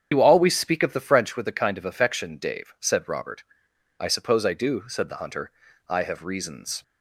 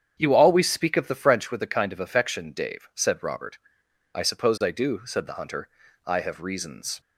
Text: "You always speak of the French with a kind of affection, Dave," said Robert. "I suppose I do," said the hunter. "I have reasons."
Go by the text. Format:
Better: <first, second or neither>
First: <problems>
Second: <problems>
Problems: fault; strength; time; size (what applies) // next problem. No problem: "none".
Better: second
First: loses the start of "You"; at 0.1 s; 50 ms // starts louder than the rest; strong; until 1.1 s; 8 dB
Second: starts louder than the rest; strong; until 1.2 s; 8 dB